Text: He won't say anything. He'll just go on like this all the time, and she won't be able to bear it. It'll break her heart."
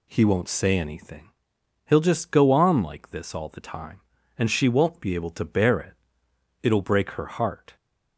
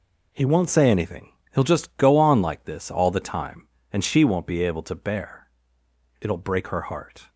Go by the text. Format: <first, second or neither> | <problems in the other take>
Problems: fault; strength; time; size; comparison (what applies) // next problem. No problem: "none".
first | skips "it"; at 5.8 s